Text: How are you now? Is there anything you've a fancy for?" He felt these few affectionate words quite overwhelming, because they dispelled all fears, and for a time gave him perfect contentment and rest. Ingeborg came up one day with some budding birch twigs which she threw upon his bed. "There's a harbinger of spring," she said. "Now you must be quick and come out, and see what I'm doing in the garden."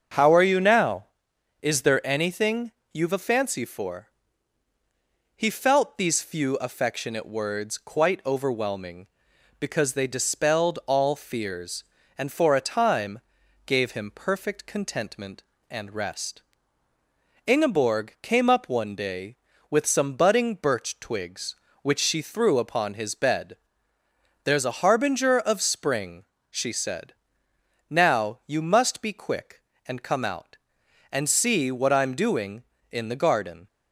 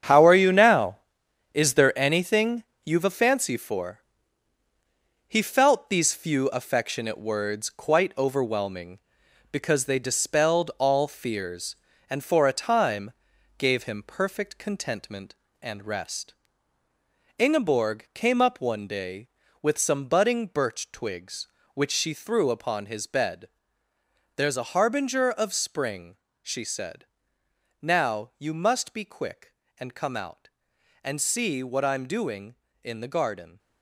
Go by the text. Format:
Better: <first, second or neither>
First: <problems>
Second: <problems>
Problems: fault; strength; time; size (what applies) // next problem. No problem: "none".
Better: first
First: starts louder than the rest; until 1.7 s; 7 dB // pauses between "anything" and "you've"; slight; at 2.7 s; 0.20 s long // pauses between "time" and "gave"; at 13.2 s; 0.44 s long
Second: gets quieter; strong; throughout; 10 dB // starts louder than the rest; strong; until 1.6 s; 8.5 dB // pauses between "anything" and "you've"; slight; at 2.6 s; 0.20 s long // pauses between "time" and "gave"; at 13.1 s; 0.44 s long